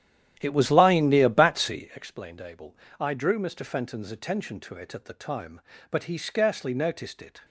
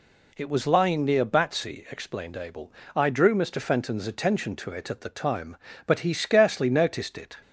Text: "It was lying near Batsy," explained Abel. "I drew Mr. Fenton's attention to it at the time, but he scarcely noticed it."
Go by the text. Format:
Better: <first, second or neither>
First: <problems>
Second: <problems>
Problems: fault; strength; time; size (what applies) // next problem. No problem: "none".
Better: second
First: starts louder than the rest; strong; until 2.0 s; 11 dB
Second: none